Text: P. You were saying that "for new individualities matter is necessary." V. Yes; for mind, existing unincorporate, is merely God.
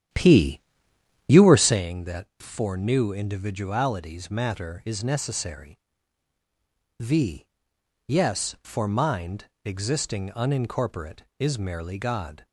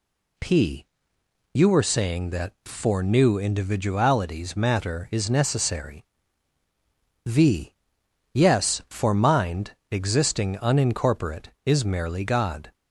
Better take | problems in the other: second | starts louder than the rest; strong; until 1.8 s; 10.5 dB

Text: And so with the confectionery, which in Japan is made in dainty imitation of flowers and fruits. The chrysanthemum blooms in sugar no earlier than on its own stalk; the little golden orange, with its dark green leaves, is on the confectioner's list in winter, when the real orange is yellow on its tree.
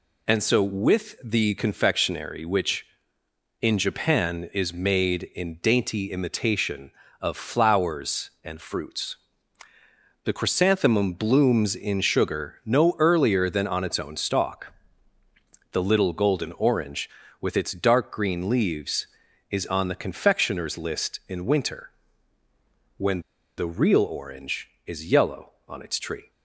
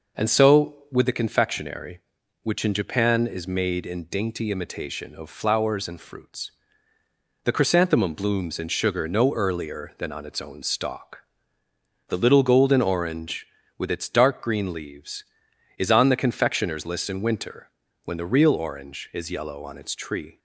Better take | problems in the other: second | pauses between "when" and "the"; at 23.2 s; 0.36 s long

